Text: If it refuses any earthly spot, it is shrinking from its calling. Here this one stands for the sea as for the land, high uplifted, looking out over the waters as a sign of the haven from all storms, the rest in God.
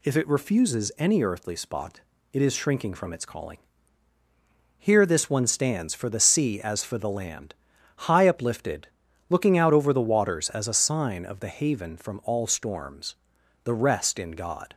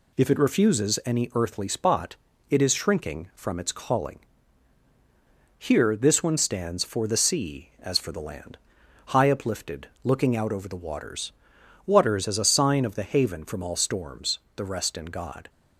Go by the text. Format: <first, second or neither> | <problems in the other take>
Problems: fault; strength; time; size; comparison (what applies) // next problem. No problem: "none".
first | says "waters" twice; at 11.8 s